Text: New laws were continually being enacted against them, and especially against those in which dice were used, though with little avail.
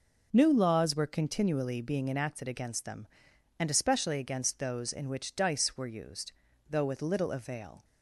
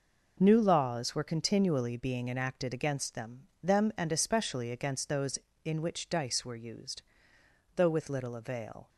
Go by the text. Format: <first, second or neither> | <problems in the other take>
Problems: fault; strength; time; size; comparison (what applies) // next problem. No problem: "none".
first | says "them" twice; at 3.6 s